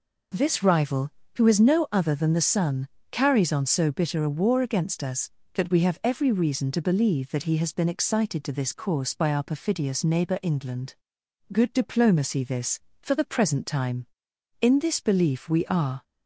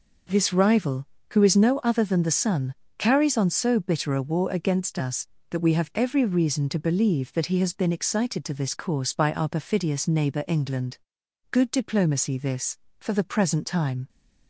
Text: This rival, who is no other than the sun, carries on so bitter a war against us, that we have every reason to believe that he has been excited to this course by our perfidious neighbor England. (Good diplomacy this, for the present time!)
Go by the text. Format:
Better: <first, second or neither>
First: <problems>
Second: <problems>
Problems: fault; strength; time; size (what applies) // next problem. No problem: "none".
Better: second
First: goes on to say "In this belief we are"; from 14.6 s on; 1.4 s long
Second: none